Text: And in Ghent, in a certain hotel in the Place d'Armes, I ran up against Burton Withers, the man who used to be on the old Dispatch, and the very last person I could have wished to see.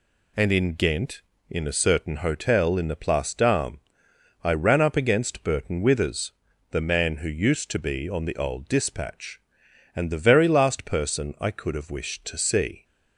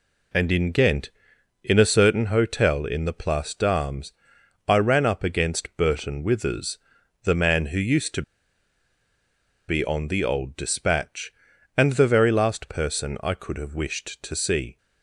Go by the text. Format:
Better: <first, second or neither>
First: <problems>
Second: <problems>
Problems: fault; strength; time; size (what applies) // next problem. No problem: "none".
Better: first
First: none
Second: pauses between "to" and "be"; strong; at 8.2 s; 1.4 s long